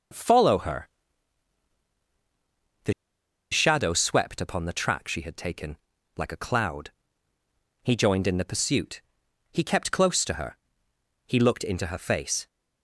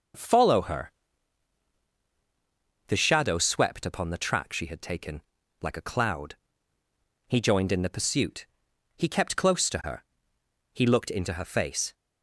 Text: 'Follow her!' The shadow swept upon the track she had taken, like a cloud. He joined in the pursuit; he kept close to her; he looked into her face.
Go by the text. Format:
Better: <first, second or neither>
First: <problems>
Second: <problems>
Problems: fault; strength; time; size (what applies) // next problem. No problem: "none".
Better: second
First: pauses between "The" and "shadow"; noticeable; at 2.9 s; 0.59 s long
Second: none